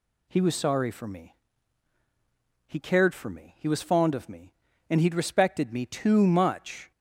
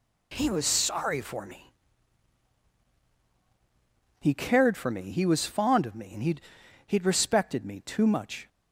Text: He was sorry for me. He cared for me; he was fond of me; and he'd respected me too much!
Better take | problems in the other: first | says "he'd" twice; at 6.8 s

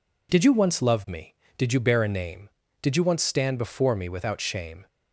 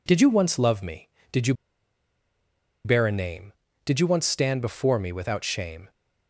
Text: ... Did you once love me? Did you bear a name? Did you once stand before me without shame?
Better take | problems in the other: first | pauses between "you" and "bear"; strong; at 1.5 s; 1.3 s long

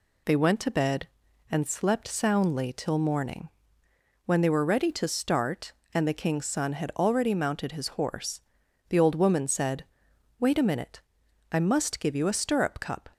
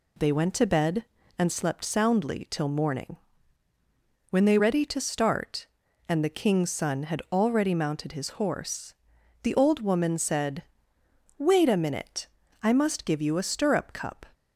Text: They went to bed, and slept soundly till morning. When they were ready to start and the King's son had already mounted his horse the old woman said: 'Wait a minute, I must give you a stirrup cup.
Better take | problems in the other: first | skips "were"; at 4.5 s // pauses between "horse" and "the"; noticeable; at 8.9 s; 0.48 s long; noticeable in the first

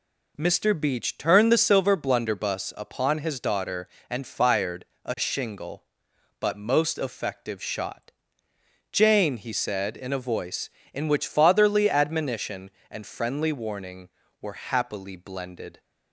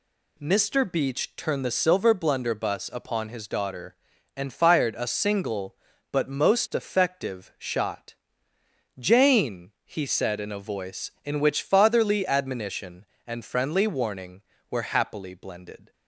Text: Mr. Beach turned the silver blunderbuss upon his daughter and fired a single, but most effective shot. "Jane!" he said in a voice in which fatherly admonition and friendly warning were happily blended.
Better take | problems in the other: second | pauses between "fired" and "a"; slight; at 4.8 s; 0.20 s long // says "shingle" for "single"; at 5.1 s

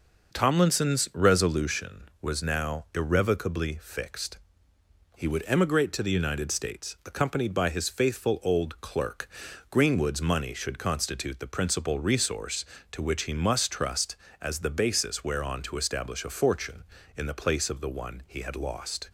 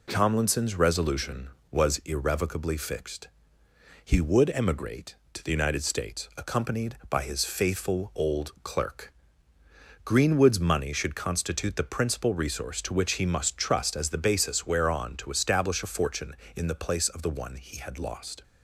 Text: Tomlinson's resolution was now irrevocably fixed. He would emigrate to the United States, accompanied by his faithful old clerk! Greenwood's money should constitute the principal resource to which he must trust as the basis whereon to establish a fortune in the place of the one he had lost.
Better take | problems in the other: first | skips "now"; at 1.9 s

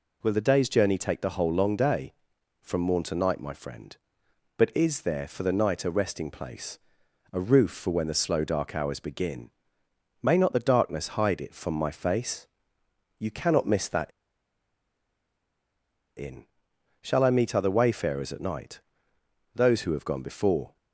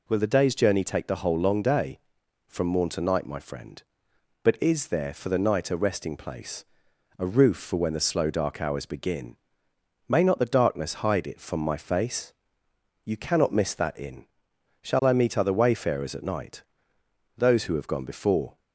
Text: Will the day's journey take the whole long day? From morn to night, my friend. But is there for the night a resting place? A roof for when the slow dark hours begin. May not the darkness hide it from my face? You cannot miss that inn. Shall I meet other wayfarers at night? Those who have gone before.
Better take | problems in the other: second | pauses between "that" and "inn"; strong; at 14.1 s; 2.0 s long

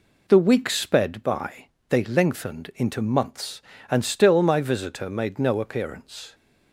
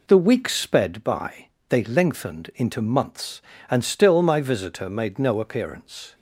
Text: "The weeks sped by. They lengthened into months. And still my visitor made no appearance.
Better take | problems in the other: neither | none

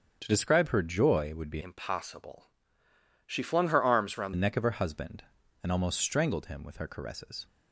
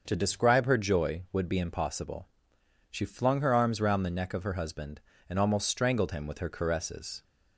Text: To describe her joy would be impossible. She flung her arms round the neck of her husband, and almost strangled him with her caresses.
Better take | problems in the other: second | starts louder than the rest; strong; until 1.2 s; 7.5 dB; also in the second // changes voice from "impossible" to "round"; from 1.6 to 4.3 s; 2.7 s long

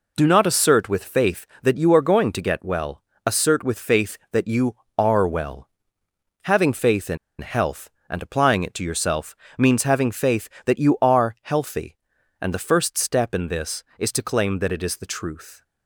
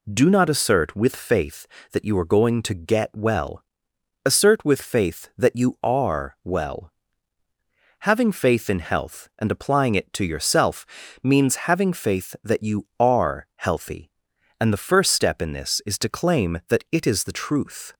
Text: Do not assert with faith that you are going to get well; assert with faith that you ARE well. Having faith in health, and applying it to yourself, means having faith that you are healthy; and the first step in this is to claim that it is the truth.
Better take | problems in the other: second | pauses between "in" and "health"; slight; at 7.1 s; 0.23 s long

